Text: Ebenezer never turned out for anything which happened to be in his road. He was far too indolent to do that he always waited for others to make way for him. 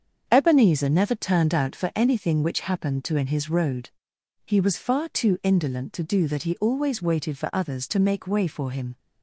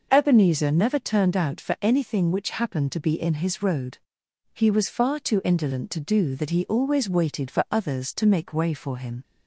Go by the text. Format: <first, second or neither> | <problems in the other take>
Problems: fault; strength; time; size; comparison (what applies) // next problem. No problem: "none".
second | starts louder than the rest; strong; until 1.2 s; 7 dB // skips "be"; at 3.1 s